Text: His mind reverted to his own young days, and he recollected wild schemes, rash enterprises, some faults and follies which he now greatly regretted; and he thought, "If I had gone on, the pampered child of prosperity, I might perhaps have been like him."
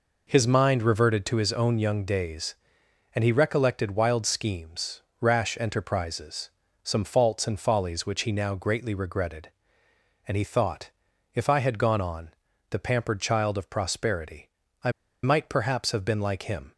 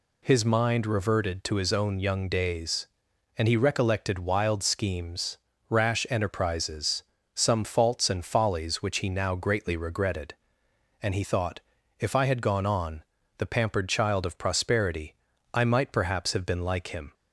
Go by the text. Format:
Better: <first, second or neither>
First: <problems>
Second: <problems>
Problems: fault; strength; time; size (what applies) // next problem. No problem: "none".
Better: second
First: pauses between "I" and "might"; slight; at 14.9 s; 0.33 s long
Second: none